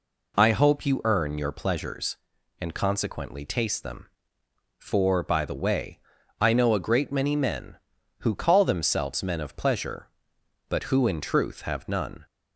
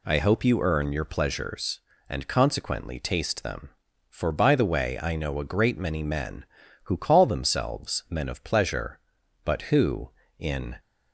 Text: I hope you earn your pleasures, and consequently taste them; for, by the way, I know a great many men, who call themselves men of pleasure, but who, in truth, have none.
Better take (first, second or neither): first